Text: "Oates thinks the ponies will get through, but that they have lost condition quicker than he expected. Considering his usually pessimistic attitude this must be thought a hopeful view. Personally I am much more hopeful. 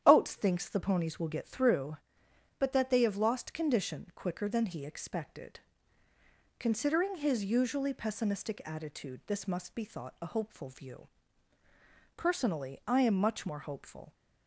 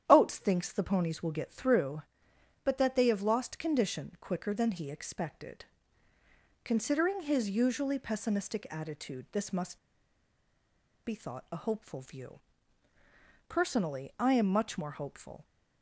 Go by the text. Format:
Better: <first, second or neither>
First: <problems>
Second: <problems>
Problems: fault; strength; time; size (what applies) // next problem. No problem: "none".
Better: first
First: starts louder than the rest; strong; until 1.0 s; 10 dB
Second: starts louder than the rest; strong; until 1.0 s; 10 dB // pauses between "must" and "be"; strong; at 9.7 s; 1.2 s long